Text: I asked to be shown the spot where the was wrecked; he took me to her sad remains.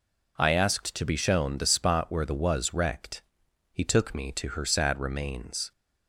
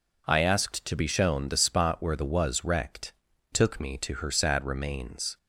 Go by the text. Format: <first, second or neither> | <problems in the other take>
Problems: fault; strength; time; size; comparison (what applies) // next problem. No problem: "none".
first | skips "he"; at 3.3 s